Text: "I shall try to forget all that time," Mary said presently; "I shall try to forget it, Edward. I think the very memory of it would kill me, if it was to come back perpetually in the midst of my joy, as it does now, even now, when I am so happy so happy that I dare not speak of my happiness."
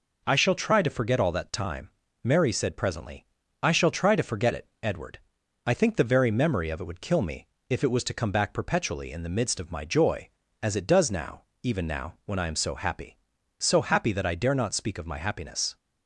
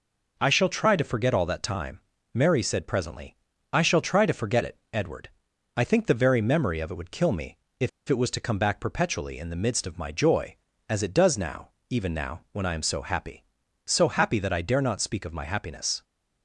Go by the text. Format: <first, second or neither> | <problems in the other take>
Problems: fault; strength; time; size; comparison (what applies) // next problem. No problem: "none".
first | pauses between "if" and "it"; slight; at 7.8 s; 0.19 s long